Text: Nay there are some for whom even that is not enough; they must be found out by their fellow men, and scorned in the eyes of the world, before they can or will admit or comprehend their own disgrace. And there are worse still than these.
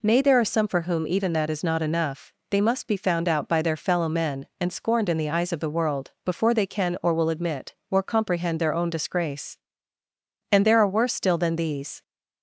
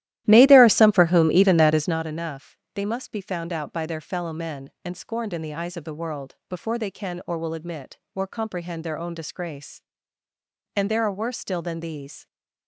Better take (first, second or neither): first